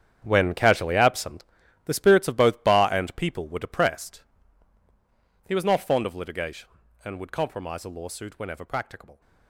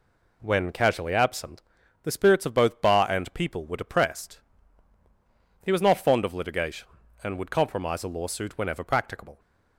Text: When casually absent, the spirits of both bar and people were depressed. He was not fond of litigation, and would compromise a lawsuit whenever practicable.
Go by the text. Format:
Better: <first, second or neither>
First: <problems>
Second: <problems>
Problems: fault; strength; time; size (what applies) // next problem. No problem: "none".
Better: second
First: gets quieter; strong; throughout; 14.5 dB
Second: none